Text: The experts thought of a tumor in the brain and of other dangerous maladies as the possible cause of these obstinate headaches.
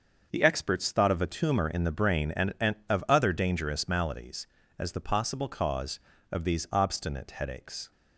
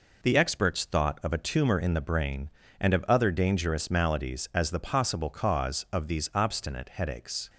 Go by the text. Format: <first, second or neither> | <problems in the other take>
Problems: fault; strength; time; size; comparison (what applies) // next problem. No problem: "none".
second | starts louder than the rest; until 1.3 s; 6.5 dB // says "and" twice; at 2.6 s